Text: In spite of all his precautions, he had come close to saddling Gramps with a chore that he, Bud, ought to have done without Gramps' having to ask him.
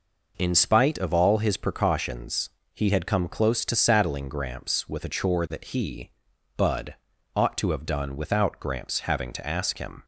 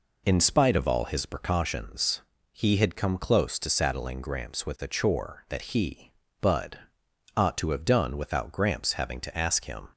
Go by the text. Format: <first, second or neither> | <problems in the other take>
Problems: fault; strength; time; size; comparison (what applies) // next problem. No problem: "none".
neither | none